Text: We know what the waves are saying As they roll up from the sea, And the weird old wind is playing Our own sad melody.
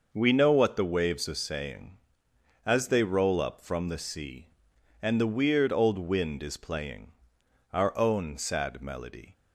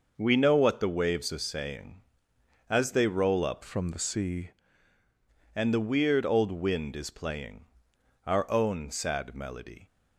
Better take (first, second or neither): first